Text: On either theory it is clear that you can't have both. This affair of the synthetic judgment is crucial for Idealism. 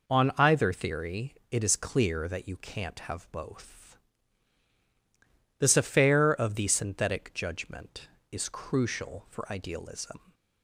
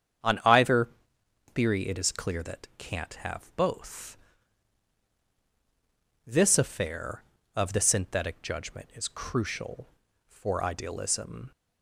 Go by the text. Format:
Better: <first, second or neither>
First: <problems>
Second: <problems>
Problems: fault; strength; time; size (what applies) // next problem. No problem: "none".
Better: first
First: none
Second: starts louder than the rest; strong; until 1.9 s; 8 dB // pauses between "either" and "theory"; noticeable; at 0.8 s; 0.64 s long // skips "you"; at 2.7 s